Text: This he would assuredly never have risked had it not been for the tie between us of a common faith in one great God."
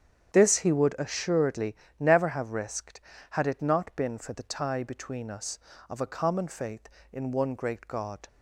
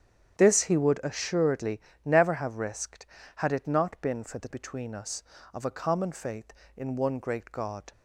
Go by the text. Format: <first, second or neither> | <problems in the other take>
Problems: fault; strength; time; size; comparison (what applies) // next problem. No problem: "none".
first | starts louder than the rest; strong; until 1.4 s; 9 dB; strong in the first // pauses between "assuredly" and "never"; slight; at 1.7 s; 0.28 s long; slight in the first // skips "tie"; at 4.4 s